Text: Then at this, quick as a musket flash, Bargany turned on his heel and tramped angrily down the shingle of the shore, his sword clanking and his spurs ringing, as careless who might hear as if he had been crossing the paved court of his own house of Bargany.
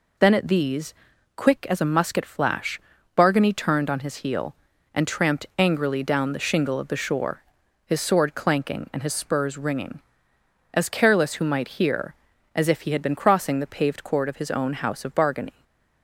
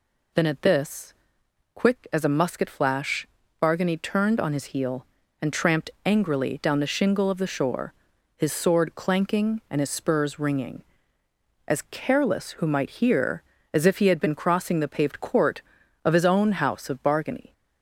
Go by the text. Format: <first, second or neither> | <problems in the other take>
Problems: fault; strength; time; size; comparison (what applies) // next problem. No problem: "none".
second | says "these" for "this"; at 0.4 s // stays silent after the last word; slight; from 15.5 s on; 0.5 s long